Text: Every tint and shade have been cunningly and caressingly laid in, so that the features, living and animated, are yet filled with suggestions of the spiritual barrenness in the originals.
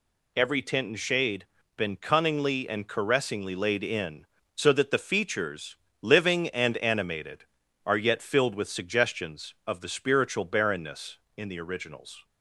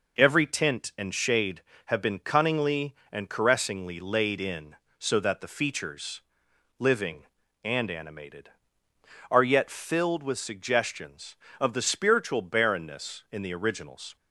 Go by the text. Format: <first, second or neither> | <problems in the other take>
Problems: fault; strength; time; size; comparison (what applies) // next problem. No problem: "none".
second | skips "have"; at 1.6 s